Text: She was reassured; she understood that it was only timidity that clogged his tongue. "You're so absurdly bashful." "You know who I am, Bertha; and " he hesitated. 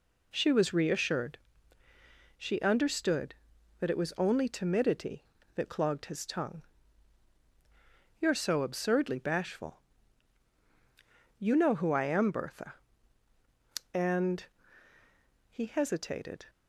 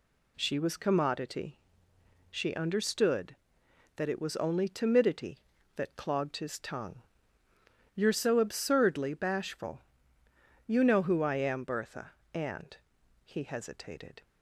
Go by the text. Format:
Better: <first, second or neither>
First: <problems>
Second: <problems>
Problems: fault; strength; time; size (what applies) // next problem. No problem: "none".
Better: first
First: none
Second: says "commodity" for "reassured"; at 0.7 s